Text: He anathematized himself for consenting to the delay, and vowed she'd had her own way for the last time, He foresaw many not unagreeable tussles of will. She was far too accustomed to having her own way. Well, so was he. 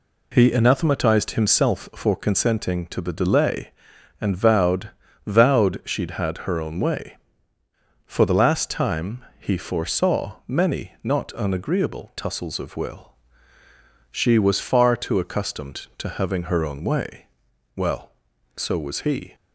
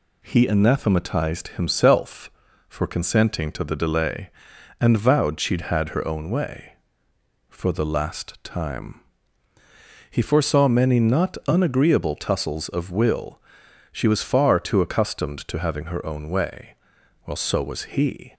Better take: second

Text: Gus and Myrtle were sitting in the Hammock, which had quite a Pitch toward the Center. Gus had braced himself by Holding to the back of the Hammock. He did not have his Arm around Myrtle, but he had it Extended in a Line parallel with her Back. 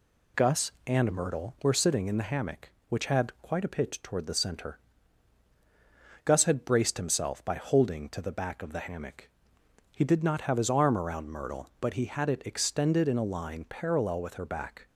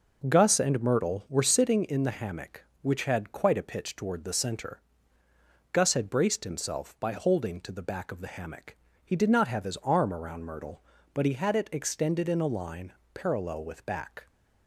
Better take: first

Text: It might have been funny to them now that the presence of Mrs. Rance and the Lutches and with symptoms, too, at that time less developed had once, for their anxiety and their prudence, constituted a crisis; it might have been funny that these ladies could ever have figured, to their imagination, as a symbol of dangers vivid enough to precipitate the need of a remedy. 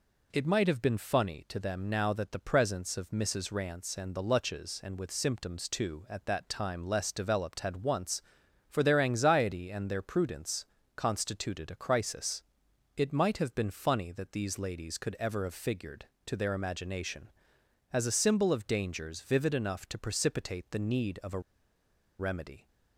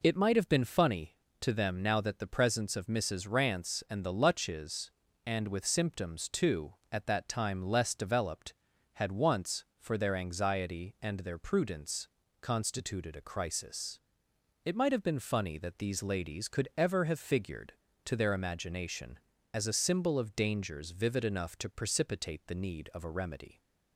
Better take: second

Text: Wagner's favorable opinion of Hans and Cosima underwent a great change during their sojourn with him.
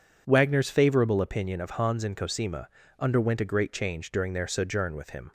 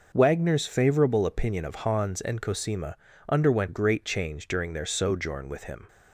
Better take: first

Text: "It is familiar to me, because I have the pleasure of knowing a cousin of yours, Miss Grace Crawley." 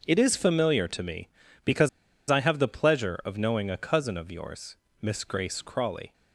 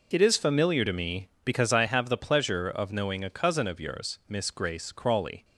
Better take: second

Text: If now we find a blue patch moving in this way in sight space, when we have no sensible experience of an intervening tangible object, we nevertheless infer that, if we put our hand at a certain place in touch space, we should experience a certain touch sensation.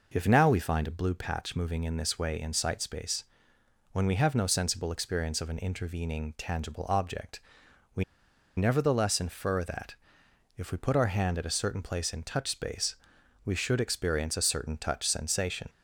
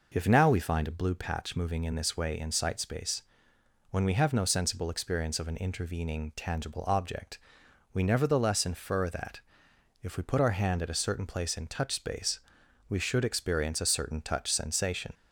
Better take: second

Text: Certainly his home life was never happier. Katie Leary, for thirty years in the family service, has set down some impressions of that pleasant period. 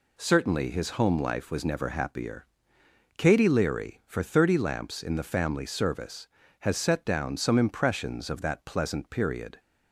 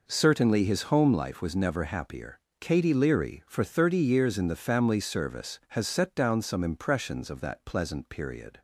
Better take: second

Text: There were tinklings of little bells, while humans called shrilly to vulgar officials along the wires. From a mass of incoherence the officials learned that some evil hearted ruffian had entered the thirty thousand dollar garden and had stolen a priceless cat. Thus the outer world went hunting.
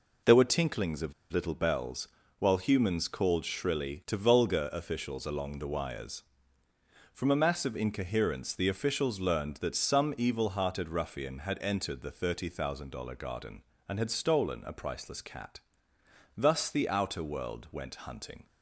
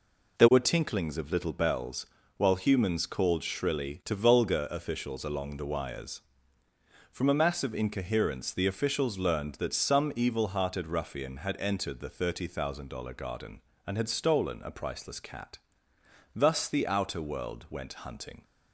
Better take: second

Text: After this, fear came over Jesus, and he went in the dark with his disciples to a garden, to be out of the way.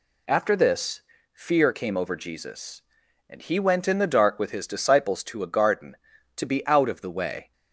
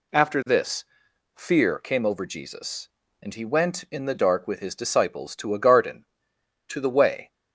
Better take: first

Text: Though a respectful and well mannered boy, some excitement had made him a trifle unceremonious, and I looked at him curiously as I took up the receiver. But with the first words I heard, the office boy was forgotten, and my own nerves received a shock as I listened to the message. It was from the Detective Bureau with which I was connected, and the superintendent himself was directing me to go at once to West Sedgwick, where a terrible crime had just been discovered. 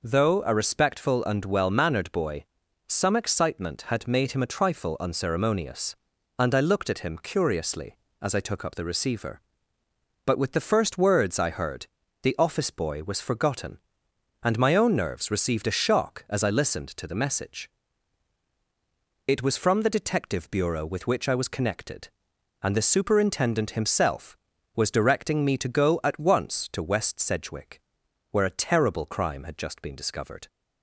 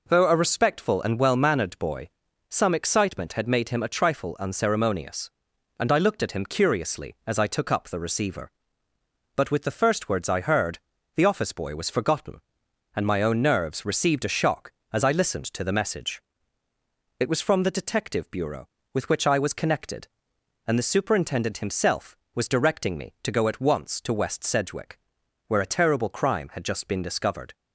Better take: neither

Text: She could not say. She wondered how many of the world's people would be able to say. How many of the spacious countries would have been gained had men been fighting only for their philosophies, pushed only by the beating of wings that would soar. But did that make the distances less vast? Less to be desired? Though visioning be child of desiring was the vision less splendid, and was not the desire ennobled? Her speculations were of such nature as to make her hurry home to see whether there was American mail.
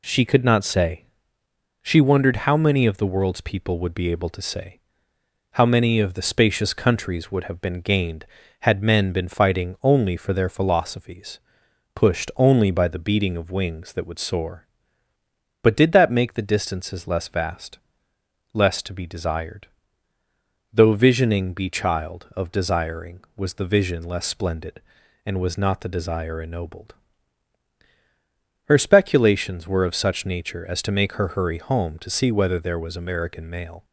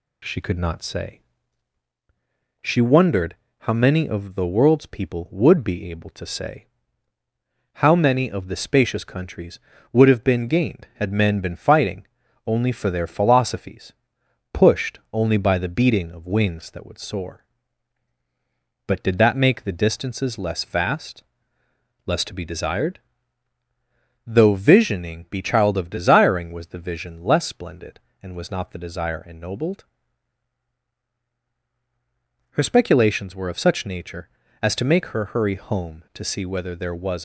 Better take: first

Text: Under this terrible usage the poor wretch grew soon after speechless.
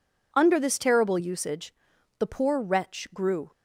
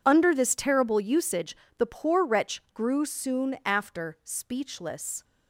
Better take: second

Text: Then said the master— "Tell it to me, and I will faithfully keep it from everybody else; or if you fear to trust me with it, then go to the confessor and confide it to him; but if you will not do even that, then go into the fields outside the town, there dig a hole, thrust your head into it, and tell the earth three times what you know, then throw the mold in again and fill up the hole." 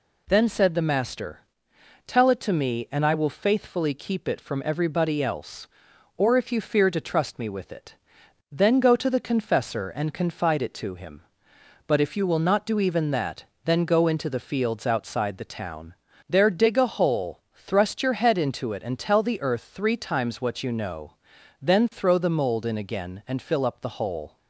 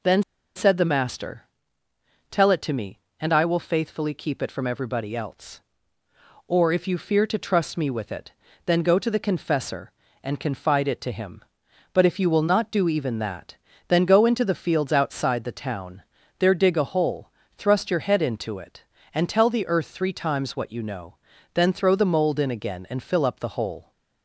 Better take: first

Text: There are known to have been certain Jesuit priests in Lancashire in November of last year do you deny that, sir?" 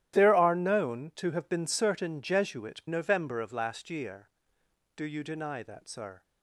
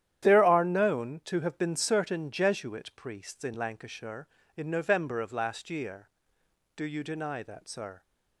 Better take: second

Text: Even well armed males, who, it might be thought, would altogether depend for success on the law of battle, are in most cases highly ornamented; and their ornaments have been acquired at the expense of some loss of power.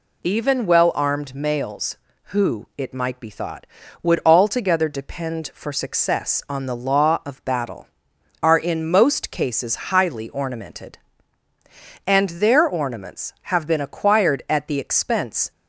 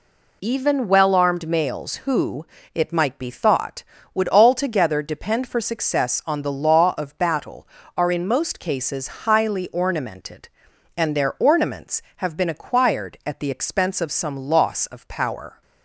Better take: second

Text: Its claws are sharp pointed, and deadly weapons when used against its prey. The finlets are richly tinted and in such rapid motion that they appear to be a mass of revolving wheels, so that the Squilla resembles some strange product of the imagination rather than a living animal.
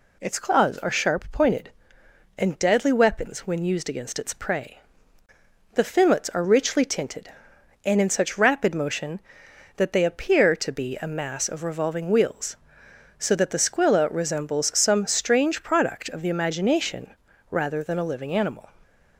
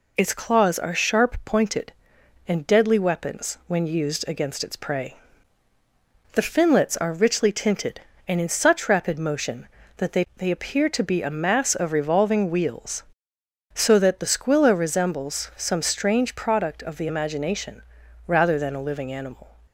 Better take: first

